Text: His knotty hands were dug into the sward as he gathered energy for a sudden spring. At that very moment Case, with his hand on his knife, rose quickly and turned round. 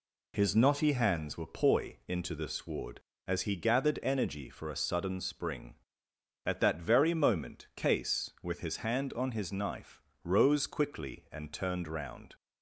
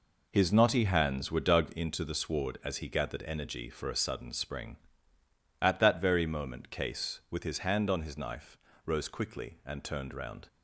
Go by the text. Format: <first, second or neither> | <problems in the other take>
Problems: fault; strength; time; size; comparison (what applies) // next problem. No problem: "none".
second | says "poi" for "dug"; at 1.4 s